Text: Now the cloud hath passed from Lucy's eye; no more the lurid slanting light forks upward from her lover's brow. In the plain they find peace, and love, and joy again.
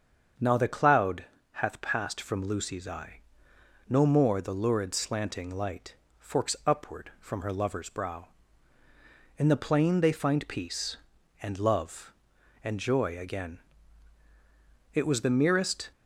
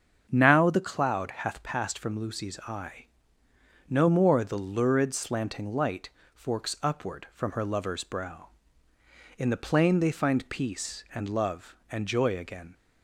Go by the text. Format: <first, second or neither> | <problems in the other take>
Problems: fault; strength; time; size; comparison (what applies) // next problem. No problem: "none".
second | starts louder than the rest; until 1.6 s; 7 dB; strong in the second // pauses between "cloud" and "hath"; slight; at 1.2 s; 0.29 s long // pauses between "light" and "forks"; slight; at 5.9 s; 0.24 s long; slight in the second // goes on to say "It was the merest"; noticeable; from 14.9 s on; 0.98 s long